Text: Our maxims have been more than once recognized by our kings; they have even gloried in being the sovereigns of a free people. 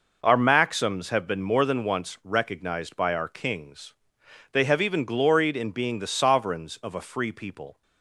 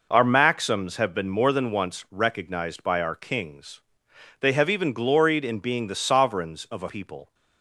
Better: first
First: none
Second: skips "free"; at 6.8 s

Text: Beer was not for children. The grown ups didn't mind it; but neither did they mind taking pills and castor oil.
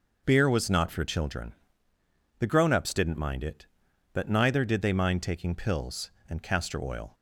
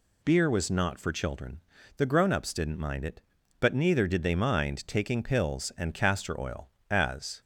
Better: first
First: none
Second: goes on to say "As"; from 6.9 s on; 0.50 s long

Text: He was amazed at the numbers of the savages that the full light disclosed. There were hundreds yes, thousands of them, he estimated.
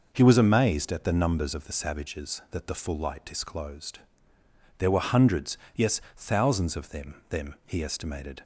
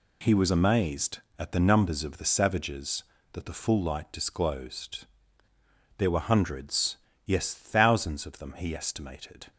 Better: second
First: pauses between "hundreds" and "yes"; slight; at 5.5 s; 0.20 s long // says "them" twice; at 7.2 s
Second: pauses between "hundreds" and "yes"; slight; at 6.9 s; 0.28 s long

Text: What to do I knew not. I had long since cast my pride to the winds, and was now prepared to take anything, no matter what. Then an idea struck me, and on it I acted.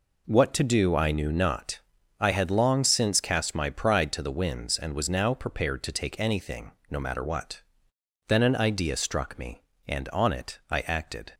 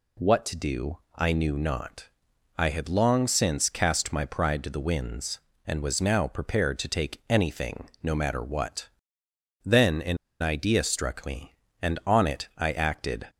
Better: first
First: none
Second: pauses between "do" and "I"; slight; at 0.9 s; 0.16 s long // pauses between "an" and "idea"; slight; at 10.1 s; 0.24 s long

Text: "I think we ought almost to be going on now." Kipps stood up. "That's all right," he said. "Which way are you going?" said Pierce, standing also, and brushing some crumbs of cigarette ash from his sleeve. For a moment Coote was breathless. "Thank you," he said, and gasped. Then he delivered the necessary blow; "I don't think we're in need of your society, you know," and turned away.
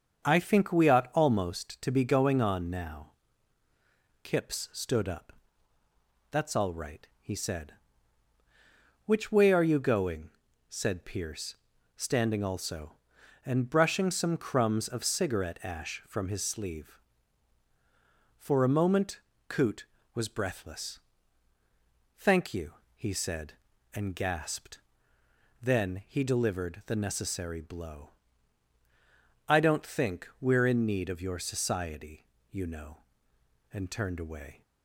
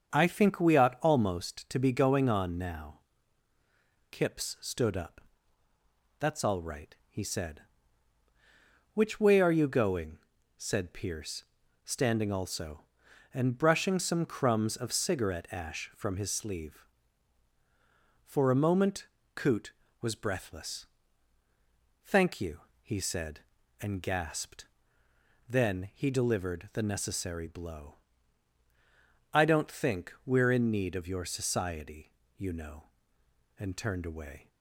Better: neither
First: starts louder than the rest; until 1.2 s; 7 dB // pauses between "moment" and "Coote"; slight; at 19.1 s; 0.28 s long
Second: starts louder than the rest; until 1.1 s; 7 dB // pauses between "moment" and "Coote"; slight; at 19.0 s; 0.28 s long

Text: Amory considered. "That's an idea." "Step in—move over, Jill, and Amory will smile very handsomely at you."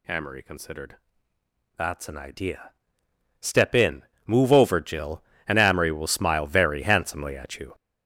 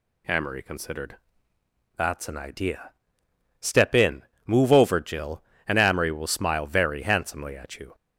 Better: second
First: gets louder; strong; throughout; 9.5 dB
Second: none

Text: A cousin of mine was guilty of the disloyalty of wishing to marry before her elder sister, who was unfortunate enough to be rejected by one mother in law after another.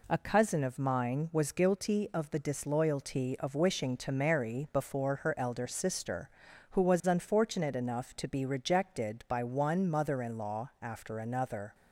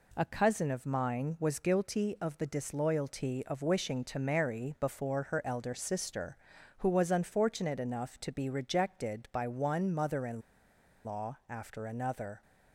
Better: first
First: none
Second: pauses between "in" and "law"; noticeable; at 10.4 s; 0.63 s long

